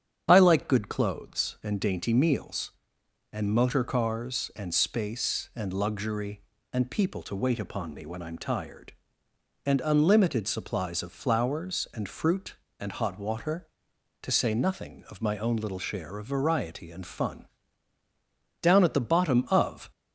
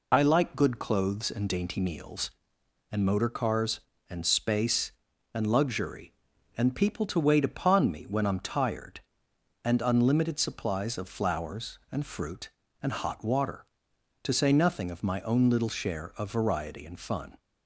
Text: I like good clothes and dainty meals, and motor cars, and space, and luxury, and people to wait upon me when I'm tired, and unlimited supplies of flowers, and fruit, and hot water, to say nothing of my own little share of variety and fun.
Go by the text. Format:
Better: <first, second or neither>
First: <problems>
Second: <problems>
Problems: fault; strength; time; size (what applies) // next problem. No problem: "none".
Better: second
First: starts louder than the rest; strong; until 1.3 s; 8.5 dB // goes on to say "Down at the bottom of"; noticeable; from 18.6 s on; 1.2 s long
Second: none